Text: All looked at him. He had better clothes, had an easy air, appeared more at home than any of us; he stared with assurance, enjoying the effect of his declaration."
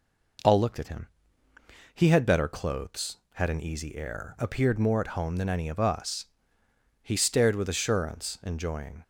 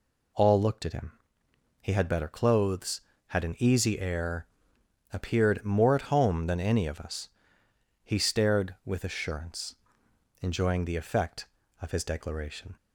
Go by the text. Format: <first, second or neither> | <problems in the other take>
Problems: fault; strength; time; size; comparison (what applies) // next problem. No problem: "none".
second | stops before "the effect of his declaration"; at 9.0 s